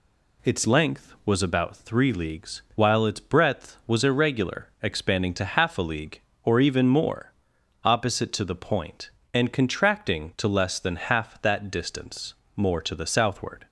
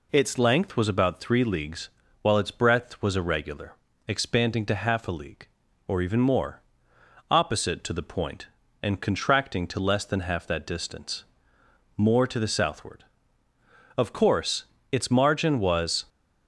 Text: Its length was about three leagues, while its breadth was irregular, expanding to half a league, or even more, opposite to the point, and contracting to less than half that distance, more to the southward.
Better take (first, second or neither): first